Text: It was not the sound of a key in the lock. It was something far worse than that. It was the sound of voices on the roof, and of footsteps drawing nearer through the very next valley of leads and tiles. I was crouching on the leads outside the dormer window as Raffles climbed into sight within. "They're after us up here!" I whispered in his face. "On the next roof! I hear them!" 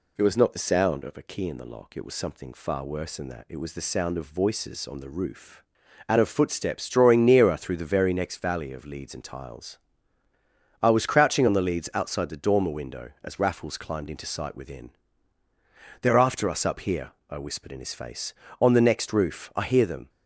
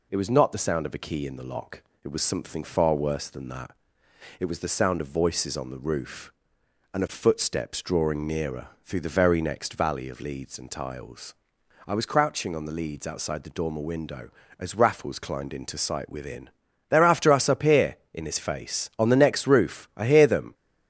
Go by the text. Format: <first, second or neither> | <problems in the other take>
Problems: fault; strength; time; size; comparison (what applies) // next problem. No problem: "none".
first | pauses between "nearer" and "through"; slight; at 8.6 s; 0.16 s long // skips "I whispered"; at 18.0 s